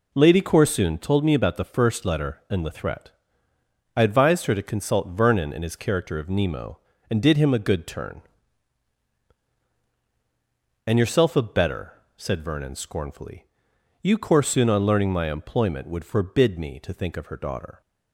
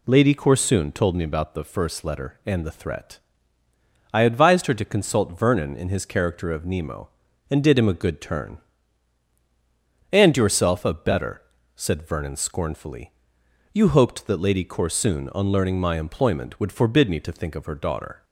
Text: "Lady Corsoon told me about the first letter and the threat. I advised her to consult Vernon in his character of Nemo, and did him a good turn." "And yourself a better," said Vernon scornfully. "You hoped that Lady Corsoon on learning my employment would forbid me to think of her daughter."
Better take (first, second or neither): second